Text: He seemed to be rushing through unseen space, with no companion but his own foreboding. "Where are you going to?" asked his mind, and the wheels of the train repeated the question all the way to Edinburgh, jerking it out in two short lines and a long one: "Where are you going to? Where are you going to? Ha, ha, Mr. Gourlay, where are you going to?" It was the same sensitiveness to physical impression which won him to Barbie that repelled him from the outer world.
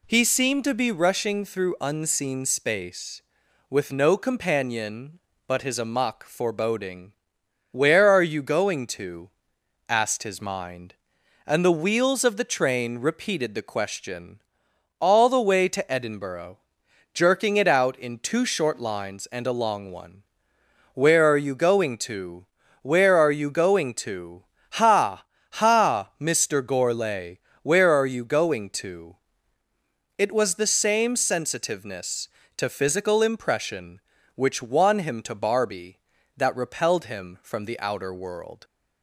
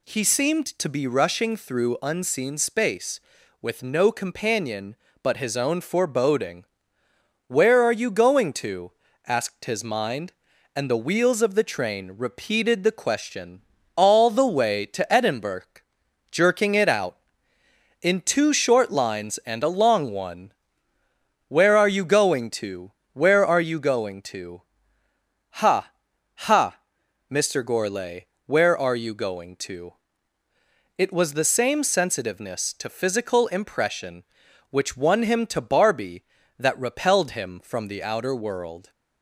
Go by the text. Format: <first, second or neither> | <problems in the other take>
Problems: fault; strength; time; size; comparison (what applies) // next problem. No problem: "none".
second | says "amok" for "own"; at 5.7 s // pauses between "question" and "all"; noticeable; at 14.4 s; 0.58 s long; slight in the second